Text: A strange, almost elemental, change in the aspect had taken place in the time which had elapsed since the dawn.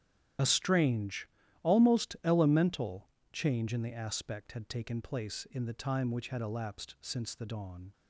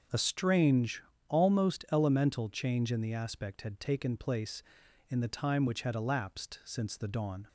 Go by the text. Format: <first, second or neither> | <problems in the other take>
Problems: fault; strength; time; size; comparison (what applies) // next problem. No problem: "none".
second | loses the start of "A"; at 0.3 s; 30 ms // starts louder than the rest; strong; until 1.7 s; 10.5 dB; also in the second